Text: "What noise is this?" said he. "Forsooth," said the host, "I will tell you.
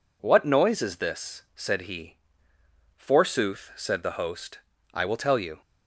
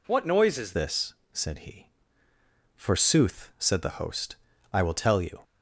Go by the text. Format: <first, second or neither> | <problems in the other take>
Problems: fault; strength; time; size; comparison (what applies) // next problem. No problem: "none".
first | changes voice at "this"; from 0.7 s on; 4.7 s long